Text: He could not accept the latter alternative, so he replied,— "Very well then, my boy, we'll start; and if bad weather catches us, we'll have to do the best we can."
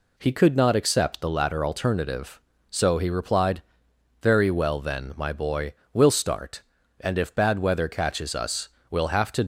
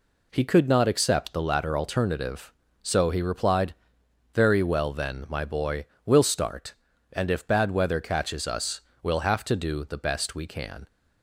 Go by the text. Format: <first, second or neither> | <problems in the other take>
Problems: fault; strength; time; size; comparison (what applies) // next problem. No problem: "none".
second | stops before "do the best we can"; at 9.4 s